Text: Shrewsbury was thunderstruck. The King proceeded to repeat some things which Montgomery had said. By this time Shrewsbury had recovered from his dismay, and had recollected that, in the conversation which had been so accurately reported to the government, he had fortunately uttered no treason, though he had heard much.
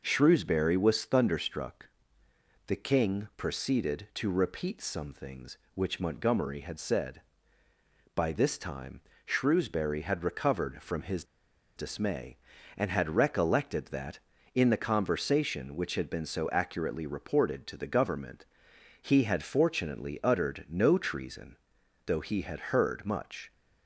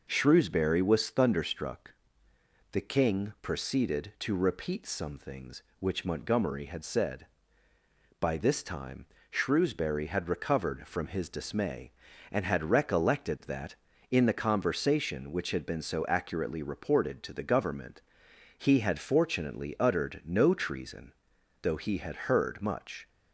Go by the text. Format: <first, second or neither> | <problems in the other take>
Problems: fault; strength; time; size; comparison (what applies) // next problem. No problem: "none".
second | pauses between "time" and "Shrewsbury"; slight; at 8.9 s; 0.24 s long; slight in the second // pauses between "his" and "dismay"; noticeable; at 11.2 s; 0.53 s long